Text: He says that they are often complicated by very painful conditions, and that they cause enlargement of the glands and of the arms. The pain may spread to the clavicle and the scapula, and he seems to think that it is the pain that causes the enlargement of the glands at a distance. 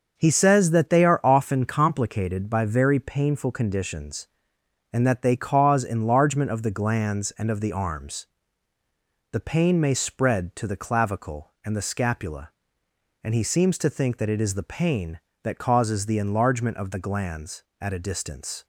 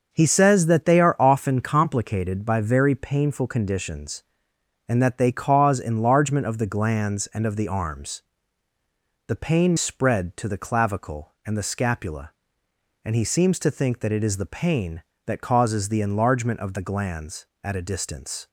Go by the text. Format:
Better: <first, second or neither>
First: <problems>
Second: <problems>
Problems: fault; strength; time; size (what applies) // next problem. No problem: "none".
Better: first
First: starts louder than the rest; until 1.1 s; 6 dB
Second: starts louder than the rest; until 1.1 s; 6 dB // skips "may"; at 9.7 s